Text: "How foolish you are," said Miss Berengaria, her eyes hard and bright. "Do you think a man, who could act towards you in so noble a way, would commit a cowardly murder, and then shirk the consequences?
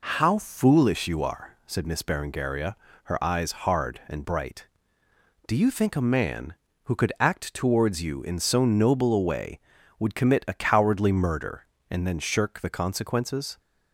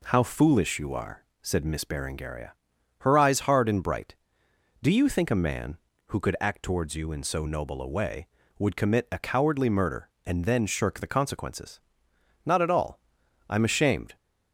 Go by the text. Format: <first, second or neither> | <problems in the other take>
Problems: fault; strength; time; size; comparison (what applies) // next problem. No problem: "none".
first | goes on to say "Not at all I'm ashamed"; strong; from 12.4 s on; 1.7 s long